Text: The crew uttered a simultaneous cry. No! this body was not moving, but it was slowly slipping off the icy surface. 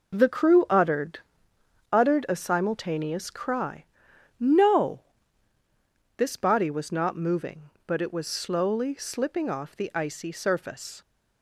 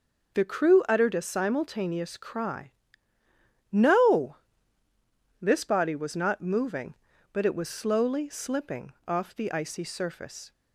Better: second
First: says "uttered" twice; at 1.9 s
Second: none

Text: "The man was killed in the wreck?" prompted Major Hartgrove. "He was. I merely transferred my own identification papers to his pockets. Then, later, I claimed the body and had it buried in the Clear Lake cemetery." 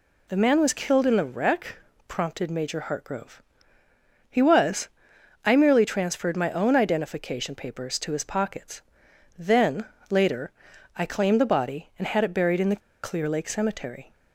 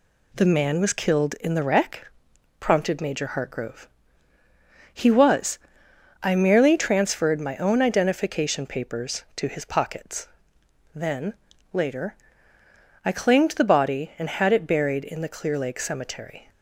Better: second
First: pauses between "the" and "Clear"; slight; at 12.8 s; 0.24 s long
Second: none

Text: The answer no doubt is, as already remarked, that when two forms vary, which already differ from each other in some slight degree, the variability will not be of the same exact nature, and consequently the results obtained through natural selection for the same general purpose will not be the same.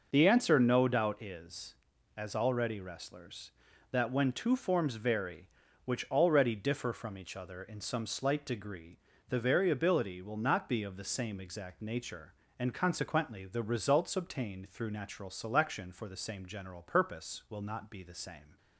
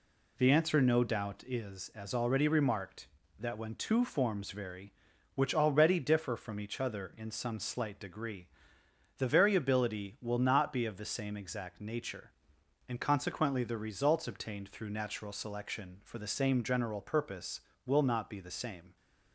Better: second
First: says "wrestlers" for "remarked"; at 2.7 s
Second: none

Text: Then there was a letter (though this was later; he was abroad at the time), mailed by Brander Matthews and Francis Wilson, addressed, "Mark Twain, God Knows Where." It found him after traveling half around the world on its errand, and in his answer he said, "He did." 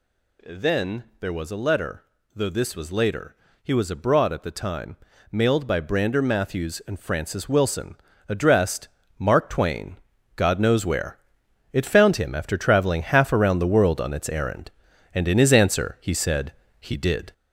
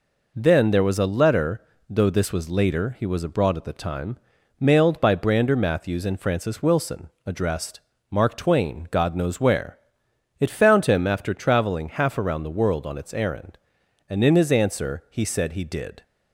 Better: second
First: gets louder; throughout; 4 dB // pauses between "Then" and "there"; slight; at 1.0 s; 0.16 s long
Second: none

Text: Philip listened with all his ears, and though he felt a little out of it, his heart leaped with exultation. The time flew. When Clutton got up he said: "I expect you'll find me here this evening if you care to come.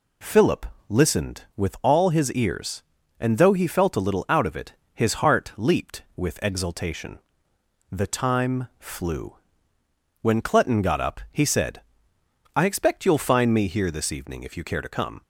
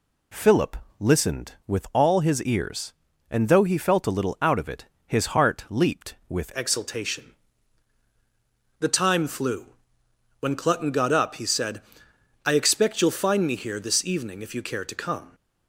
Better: first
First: pauses between "Philip" and "listened"; slight; at 0.6 s; 0.22 s long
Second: pauses between "Philip" and "listened"; slight; at 0.7 s; 0.22 s long // changes voice at "exultation"; from 6.5 s on; 8.8 s long

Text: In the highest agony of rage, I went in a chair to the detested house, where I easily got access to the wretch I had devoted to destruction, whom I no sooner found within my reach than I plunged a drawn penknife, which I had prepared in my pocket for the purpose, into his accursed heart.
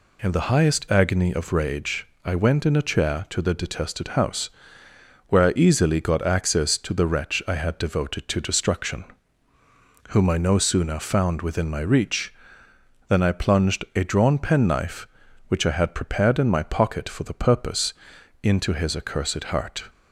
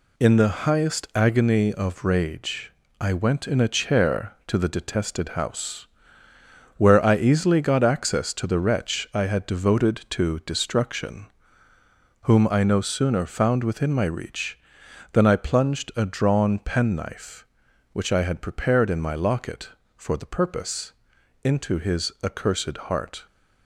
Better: first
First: none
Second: says "locket" for "pocket"; at 19.1 s

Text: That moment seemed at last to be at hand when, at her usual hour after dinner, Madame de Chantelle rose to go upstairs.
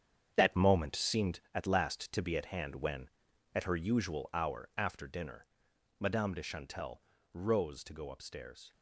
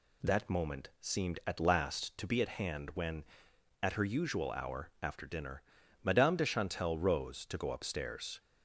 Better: second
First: gets quieter; strong; throughout; 10 dB // pauses between "Chantelle" and "rose"; slight; at 7.0 s; 0.32 s long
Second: none

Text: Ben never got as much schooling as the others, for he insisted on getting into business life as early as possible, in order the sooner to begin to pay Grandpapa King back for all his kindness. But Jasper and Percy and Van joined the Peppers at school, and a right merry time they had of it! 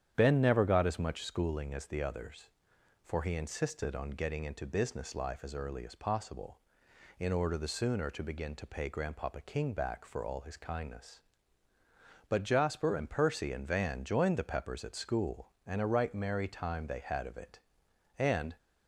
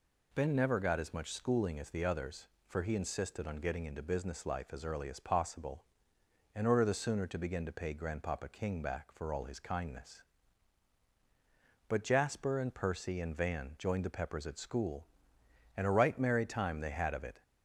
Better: second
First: starts louder than the rest; strong; until 1.1 s; 9.5 dB // goes on to say "And"; slight; from 18.1 s on; 0.38 s long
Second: none

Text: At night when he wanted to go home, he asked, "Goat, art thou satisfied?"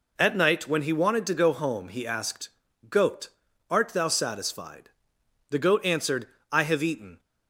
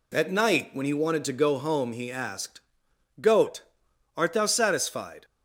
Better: second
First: goes on to say "The goat answered I have eaten"; strong; from 5.4 s on; 1.7 s long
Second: none

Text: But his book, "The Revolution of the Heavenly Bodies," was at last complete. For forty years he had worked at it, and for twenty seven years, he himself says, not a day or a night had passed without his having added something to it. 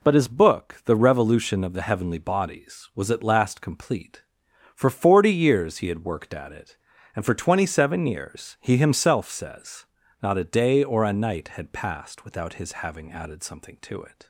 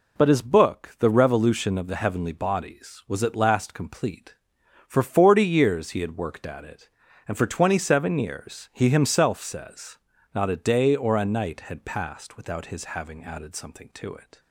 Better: neither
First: none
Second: none

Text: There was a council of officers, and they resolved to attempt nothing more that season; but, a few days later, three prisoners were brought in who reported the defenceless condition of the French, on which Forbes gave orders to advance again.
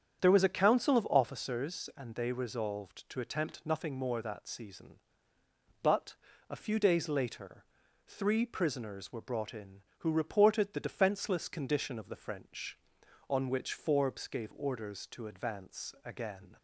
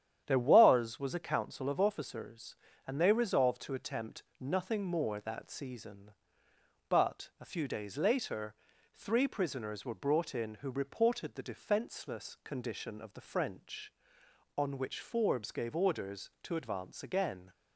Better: first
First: starts louder than the rest; strong; until 1.2 s; 8.5 dB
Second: starts louder than the rest; strong; until 1.2 s; 10 dB // says "was" twice; at 0.9 s // pauses between "attempt" and "nothing"; slight; at 4.2 s; 0.16 s long

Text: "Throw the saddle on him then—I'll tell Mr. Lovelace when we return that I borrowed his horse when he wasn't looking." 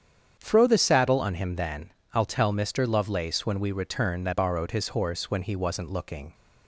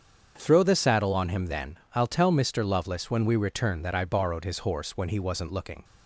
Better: second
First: starts louder than the rest; strong; until 1.4 s; 8 dB // skips "I"; at 4.3 s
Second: starts louder than the rest; strong; until 1.3 s; 7.5 dB

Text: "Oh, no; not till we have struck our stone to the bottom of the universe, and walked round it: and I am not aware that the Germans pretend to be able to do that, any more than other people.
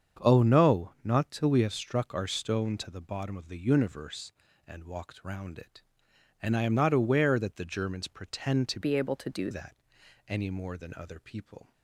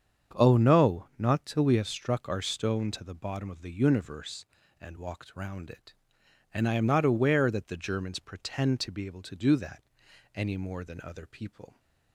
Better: second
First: starts louder than the rest; strong; until 1.3 s; 7 dB // changes voice from "be" to "do"; from 8.8 to 9.4 s; 0.6 s long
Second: starts louder than the rest; strong; until 1.4 s; 7.5 dB

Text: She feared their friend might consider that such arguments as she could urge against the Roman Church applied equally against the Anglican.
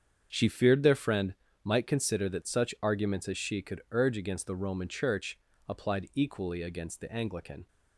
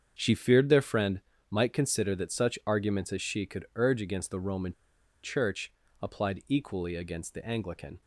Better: first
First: starts louder than the rest; strong; until 1.3 s; 7.5 dB // pauses between "friend" and "might"; slight; at 1.3 s; 0.30 s long // pauses between "Church" and "applied"; slight; at 5.3 s; 0.32 s long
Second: starts louder than the rest; strong; until 1.2 s; 7.5 dB // pauses between "friend" and "might"; slight; at 1.2 s; 0.30 s long // pauses between "Roman" and "Church"; noticeable; at 4.7 s; 0.51 s long // pauses between "Church" and "applied"; slight; at 5.7 s; 0.32 s long

